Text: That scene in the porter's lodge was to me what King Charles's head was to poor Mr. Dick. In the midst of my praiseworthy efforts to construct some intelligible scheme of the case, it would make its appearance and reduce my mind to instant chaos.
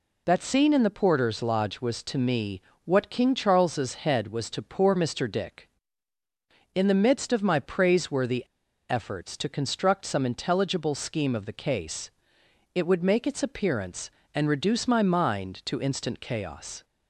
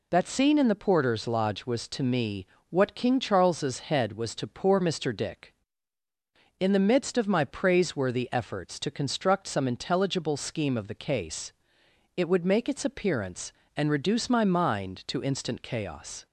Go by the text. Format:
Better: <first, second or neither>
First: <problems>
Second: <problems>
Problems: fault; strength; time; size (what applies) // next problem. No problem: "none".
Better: second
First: pauses between "me" and "what"; slight; at 2.6 s; 0.24 s long // pauses between "praiseworthy" and "efforts"; at 8.4 s; 0.44 s long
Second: pauses between "me" and "what"; slight; at 2.4 s; 0.24 s long